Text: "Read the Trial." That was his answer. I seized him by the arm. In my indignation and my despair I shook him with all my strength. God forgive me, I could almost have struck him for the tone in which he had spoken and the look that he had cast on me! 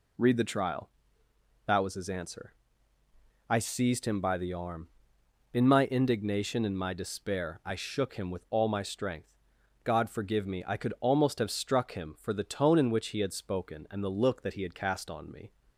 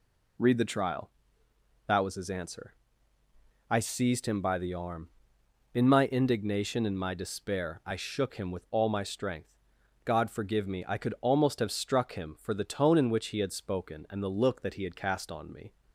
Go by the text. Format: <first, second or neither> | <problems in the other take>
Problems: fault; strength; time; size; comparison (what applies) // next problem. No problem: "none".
neither | none